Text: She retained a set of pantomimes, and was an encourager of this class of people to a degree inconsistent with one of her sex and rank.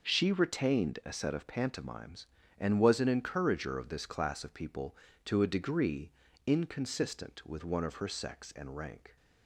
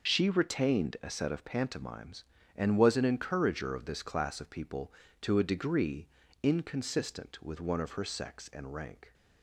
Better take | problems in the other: first | loses the start of "She"; at 0.0 s; 30 ms // pauses between "degree" and "inconsistent"; slight; at 6.0 s; 0.34 s long; slight in the first

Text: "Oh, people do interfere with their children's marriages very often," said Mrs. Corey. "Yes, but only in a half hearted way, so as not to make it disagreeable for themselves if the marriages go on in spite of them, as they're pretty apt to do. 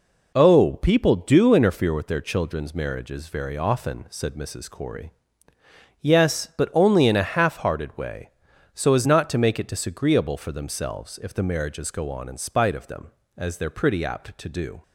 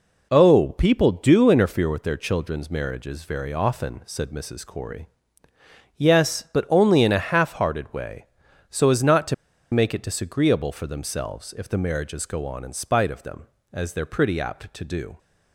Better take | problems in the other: first | pauses between "to" and "make"; at 9.3 s; 0.39 s long

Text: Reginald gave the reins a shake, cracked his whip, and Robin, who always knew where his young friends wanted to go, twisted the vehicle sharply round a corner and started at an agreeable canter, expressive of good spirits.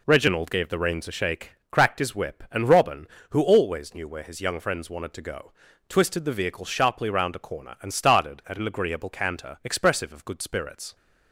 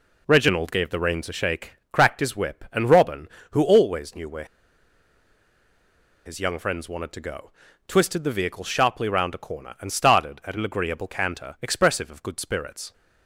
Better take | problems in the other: first | pauses between "where" and "his"; strong; at 4.4 s; 1.8 s long

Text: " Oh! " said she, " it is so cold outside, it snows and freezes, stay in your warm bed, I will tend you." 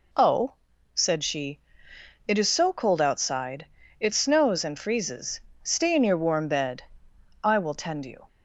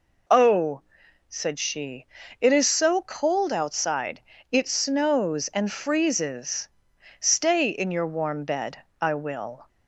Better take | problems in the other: first | stops before "tend you"; at 9.6 s

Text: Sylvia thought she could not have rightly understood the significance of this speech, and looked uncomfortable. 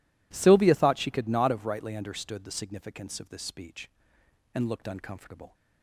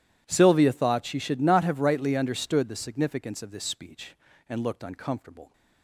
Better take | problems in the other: first | says "should" for "could"; at 1.1 s

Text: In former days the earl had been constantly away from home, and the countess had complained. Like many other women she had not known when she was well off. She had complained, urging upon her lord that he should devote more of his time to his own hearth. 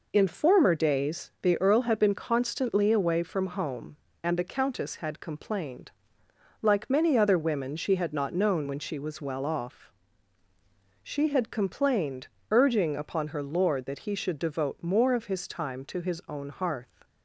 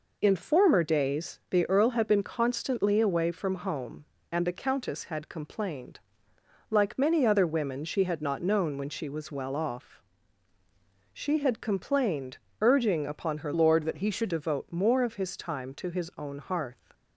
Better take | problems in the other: first | changes voice from "lord" to "should"; from 13.5 to 14.3 s; 0.8 s long

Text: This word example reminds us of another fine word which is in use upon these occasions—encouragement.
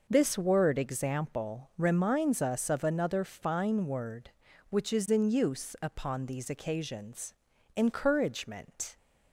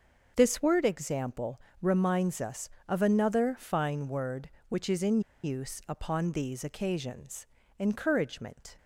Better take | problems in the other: first | starts louder than the rest; until 1.3 s; 6.5 dB // pauses between "example" and "reminds"; slight; at 1.6 s; 0.22 s long // pauses between "in" and "use"; slight; at 5.2 s; 0.23 s long

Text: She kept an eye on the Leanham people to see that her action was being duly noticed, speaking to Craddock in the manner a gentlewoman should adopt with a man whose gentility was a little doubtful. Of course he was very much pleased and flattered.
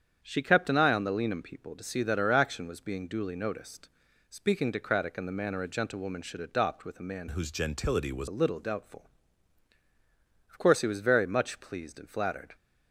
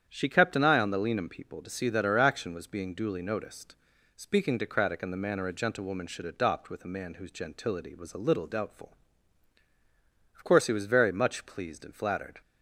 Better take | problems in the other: second | starts louder than the rest; strong; until 1.2 s; 8.5 dB; strong in the second // changes voice from "whose" to "was"; from 7.3 to 8.2 s; 0.9 s long

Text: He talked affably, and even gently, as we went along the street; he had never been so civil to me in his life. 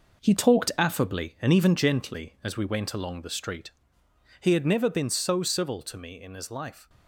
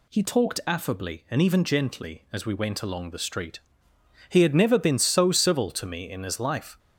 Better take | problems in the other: second | gets quieter; strong; throughout; 8 dB

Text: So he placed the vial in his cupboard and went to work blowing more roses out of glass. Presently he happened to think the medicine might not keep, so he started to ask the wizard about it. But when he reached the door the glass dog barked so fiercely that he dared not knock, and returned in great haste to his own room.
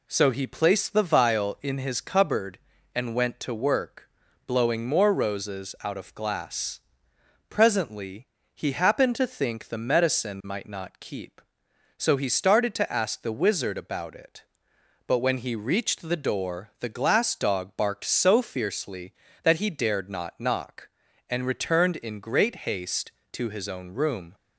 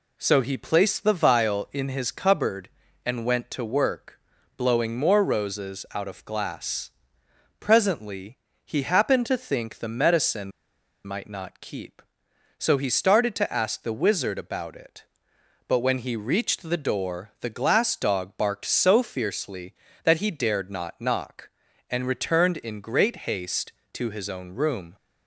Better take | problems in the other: first | pauses between "work" and "blowing"; at 4.1 s; 0.42 s long; also in the first // pauses between "Presently" and "he"; slight; at 8.3 s; 0.26 s long; slight in the first // pauses between "medicine" and "might"; noticeable; at 10.5 s; 0.54 s long

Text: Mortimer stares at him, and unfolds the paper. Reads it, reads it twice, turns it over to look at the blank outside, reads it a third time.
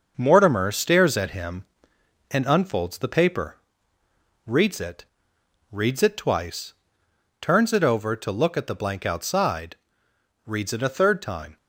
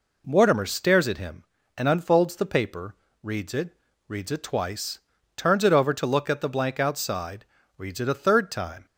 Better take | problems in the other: second | gets quieter; noticeable; throughout; 5 dB

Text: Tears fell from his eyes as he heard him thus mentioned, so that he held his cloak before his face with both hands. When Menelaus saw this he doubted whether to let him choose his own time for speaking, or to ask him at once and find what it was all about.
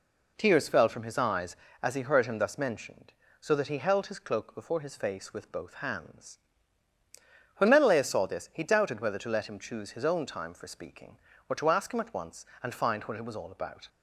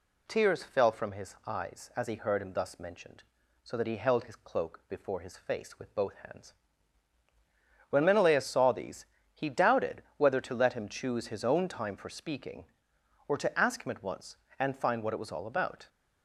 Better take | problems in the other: first | says "these" for "this"; at 8.7 s

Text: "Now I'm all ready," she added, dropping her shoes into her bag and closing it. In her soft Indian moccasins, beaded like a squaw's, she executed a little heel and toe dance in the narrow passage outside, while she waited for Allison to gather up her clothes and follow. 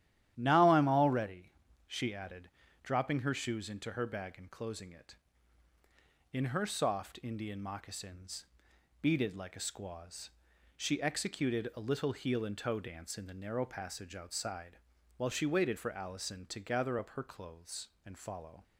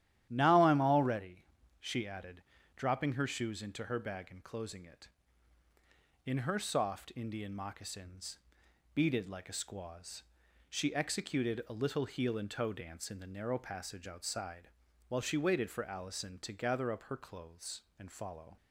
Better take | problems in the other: neither | starts louder than the rest; strong; the same in both

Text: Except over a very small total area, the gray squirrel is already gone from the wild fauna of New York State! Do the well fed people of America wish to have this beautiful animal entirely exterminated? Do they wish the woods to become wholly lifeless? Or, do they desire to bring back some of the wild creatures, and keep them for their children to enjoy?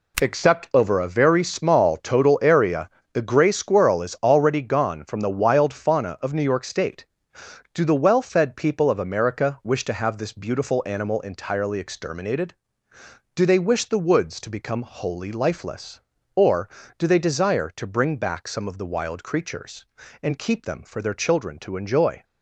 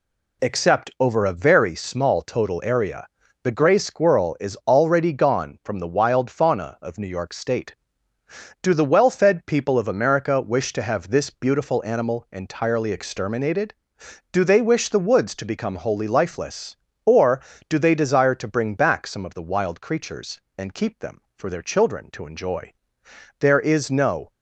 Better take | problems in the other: first | goes on to say "There is no"; noticeable; from 23.3 s on; 0.90 s long

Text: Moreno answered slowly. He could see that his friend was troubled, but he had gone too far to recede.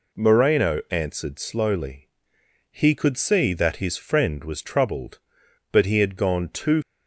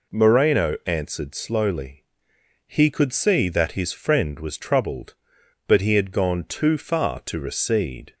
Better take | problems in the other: second | stops before "far to recede"; at 6.8 s

